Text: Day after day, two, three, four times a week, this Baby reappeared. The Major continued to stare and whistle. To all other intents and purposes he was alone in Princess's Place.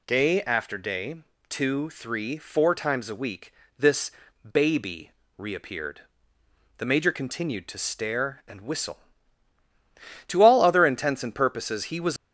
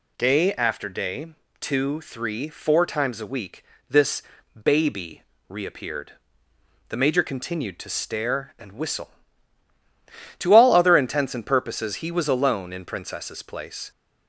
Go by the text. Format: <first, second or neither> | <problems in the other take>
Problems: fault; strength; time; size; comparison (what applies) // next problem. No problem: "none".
second | pauses between "this" and "Baby"; at 4.1 s; 0.40 s long; also in the second // pauses between "Baby" and "reappeared"; slight; at 5.1 s; 0.26 s long; slight in the second // stops before "alone in Princess's Place"; at 12.1 s